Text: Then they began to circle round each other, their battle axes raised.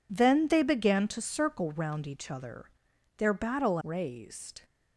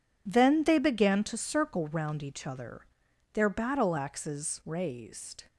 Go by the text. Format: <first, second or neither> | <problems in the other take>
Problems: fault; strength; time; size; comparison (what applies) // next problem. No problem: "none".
second | skips "axes"; at 3.8 s